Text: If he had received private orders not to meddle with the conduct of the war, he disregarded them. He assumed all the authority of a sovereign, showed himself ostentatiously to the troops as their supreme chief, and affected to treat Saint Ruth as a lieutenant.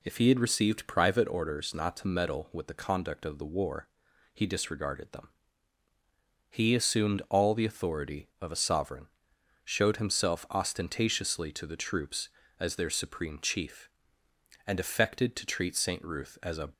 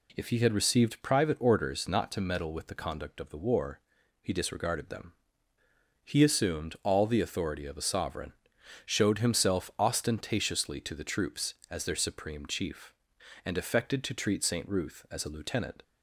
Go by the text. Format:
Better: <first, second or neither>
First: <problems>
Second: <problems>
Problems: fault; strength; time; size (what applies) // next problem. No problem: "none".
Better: second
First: stops before "lieutenant"; at 16.7 s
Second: none